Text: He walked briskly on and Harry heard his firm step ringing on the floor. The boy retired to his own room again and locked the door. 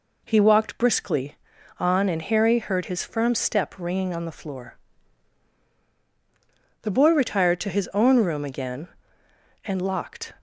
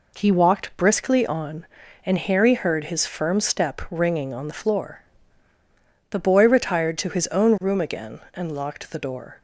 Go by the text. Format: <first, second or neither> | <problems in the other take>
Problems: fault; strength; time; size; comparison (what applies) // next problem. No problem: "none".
second | stops before "the door"; at 10.3 s